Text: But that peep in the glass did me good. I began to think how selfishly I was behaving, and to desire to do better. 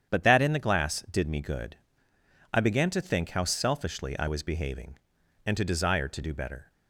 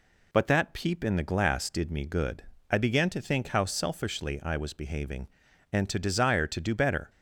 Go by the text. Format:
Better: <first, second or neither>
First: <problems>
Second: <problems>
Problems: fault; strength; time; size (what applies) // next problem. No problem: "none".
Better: second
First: starts louder than the rest; strong; until 1.1 s; 8.5 dB // skips "peep"; at 0.4 s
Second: none